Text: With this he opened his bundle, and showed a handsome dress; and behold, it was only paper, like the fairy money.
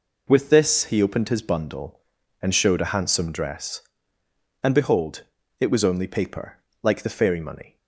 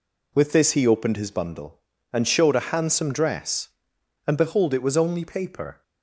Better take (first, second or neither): first